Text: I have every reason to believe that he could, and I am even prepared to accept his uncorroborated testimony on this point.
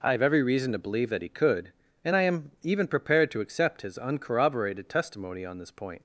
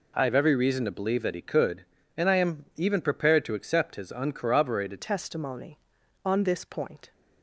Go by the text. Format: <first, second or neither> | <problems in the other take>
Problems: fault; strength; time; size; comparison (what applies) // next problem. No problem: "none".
first | changes voice at "testimony"; from 4.9 s on; 2.2 s long